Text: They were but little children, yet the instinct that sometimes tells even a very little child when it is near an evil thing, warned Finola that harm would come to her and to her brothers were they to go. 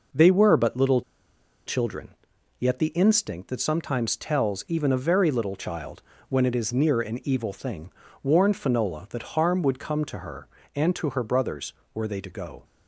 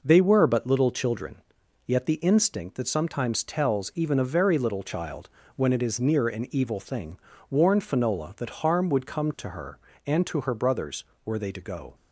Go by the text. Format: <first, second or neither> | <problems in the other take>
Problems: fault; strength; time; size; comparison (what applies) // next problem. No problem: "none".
second | pauses between "little" and "children"; noticeable; at 1.0 s; 0.65 s long // pauses between "child" and "when"; slight; at 6.0 s; 0.28 s long; slight in the second